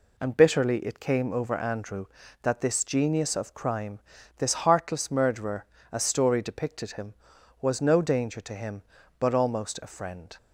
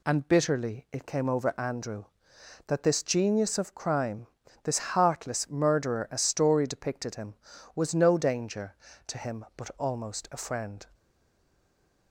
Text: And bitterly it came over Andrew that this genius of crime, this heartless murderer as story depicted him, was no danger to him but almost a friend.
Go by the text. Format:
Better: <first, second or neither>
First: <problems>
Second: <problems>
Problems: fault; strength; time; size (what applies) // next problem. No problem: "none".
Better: first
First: none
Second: stays silent after the last word; from 10.9 s on; 1.2 s long